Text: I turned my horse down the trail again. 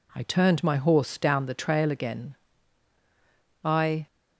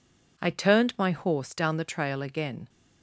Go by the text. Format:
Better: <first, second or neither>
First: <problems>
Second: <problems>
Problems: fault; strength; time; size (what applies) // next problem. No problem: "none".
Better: second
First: goes on to say "I"; slight; from 3.6 s on; 0.44 s long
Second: none